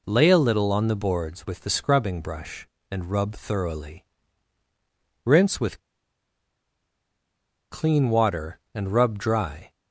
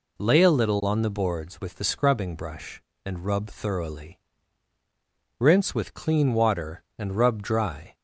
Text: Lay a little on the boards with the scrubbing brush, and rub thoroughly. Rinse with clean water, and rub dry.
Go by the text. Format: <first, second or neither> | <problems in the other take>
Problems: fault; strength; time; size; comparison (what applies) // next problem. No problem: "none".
second | pauses between "with" and "clean"; strong; at 5.7 s; 1.9 s long